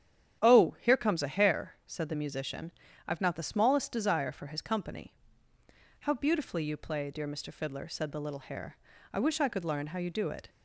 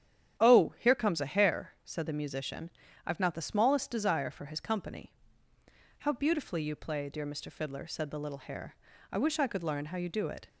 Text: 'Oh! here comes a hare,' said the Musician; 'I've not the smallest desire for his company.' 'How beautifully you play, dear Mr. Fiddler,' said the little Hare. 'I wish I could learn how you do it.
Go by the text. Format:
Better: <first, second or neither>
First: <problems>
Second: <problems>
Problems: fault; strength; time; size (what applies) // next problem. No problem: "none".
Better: neither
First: starts louder than the rest; strong; until 1.4 s; 10 dB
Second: starts louder than the rest; strong; until 1.4 s; 10 dB